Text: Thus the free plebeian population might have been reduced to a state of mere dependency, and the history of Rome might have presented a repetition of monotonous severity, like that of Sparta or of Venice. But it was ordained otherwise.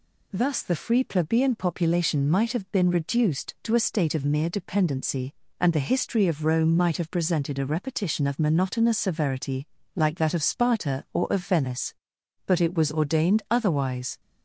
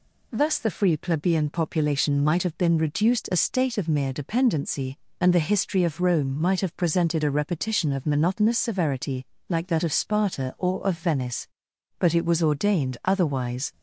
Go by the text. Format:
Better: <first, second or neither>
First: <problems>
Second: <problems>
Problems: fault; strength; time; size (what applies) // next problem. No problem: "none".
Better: first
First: none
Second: skips "to"; at 3.3 s